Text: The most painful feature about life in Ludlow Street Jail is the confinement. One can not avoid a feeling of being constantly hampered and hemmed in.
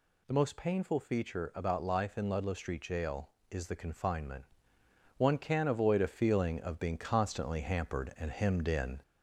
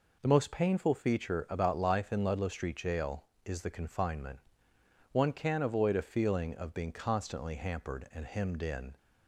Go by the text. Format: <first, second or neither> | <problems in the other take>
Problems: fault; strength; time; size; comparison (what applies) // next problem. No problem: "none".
second | gets louder; slight; throughout; 2 dB